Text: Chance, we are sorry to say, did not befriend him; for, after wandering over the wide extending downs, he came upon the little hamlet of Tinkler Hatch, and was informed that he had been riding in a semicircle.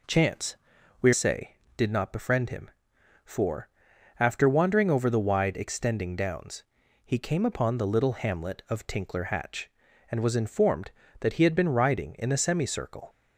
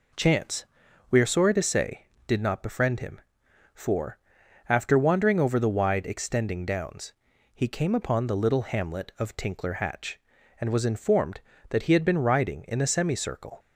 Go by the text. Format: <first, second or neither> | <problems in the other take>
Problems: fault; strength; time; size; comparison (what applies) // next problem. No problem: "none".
second | skips "are sorry to"; at 1.1 s